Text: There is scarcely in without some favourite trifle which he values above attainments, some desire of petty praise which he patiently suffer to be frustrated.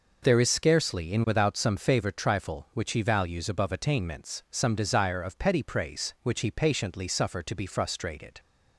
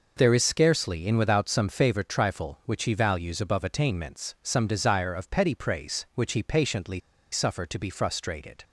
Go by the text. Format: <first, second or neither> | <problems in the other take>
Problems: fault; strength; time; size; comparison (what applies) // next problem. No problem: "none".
first | pauses between "patiently" and "suffer"; slight; at 6.9 s; 0.34 s long